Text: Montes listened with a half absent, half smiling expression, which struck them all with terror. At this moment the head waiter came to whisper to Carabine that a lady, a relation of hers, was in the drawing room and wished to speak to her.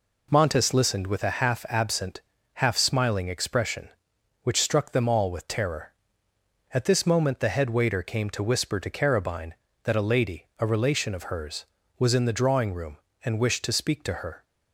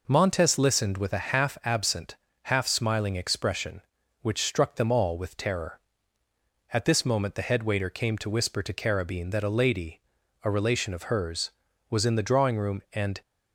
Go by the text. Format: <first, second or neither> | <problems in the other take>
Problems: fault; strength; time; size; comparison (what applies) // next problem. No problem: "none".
first | stops before "wished to speak to her"; at 13.2 s